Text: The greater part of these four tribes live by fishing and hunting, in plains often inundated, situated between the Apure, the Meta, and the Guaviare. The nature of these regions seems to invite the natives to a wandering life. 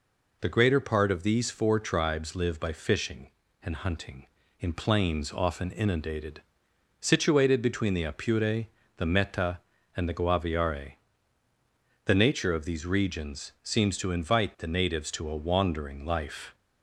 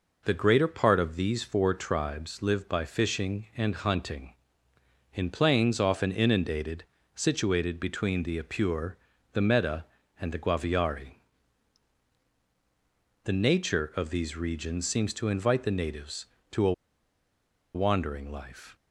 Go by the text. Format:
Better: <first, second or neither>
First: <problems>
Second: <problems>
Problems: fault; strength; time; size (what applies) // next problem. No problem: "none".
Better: first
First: none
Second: pauses between "a" and "wandering"; at 16.7 s; 1.0 s long